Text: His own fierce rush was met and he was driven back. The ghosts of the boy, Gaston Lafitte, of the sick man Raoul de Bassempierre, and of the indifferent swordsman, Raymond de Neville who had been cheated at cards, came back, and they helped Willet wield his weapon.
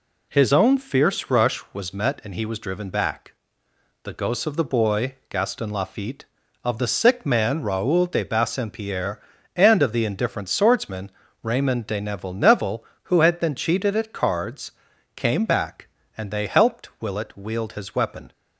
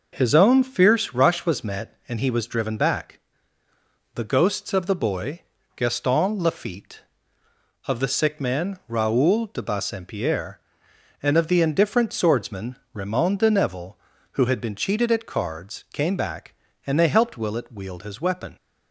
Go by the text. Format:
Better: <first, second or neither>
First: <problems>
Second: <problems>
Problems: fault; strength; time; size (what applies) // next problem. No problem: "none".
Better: second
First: says "Neville" twice; at 12.3 s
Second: none